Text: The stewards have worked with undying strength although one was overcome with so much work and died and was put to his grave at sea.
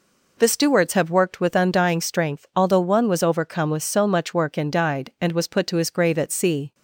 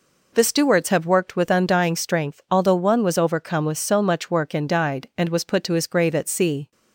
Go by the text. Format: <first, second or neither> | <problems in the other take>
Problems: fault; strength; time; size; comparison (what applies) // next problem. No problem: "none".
neither | none